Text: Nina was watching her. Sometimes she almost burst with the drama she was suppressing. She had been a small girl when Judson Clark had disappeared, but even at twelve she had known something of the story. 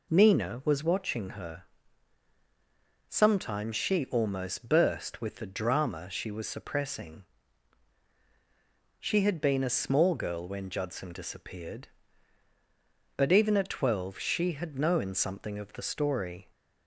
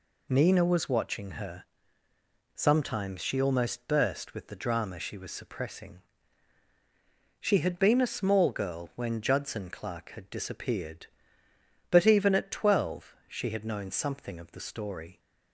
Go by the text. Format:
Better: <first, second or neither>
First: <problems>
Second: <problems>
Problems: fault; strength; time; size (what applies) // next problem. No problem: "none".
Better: second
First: skips "Clark had"; at 11.1 s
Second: none